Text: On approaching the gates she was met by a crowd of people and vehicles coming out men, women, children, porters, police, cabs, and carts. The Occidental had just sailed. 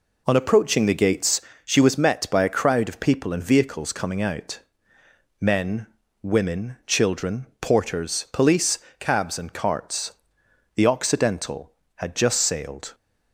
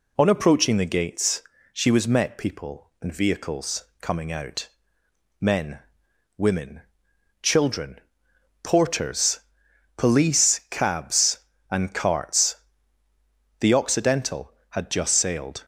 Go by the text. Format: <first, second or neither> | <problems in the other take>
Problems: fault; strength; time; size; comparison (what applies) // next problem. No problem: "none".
first | pauses between "gates" and "she"; slight; at 1.4 s; 0.30 s long; slight in the first // skips "by a crowd of"; at 2.3 s // pauses between "vehicles" and "coming"; slight; at 3.8 s; 0.16 s long // pauses between "out" and "men"; noticeable; at 4.6 s; 0.72 s long; noticeable in the first